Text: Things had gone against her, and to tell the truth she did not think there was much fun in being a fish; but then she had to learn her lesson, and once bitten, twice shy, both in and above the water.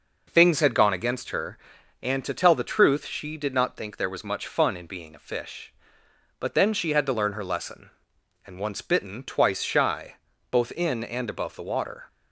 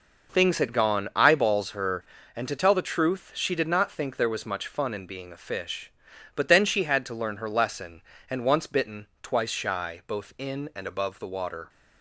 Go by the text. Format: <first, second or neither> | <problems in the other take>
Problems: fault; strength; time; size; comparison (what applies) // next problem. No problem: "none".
first | says "eyeballs" for "against"; at 1.1 s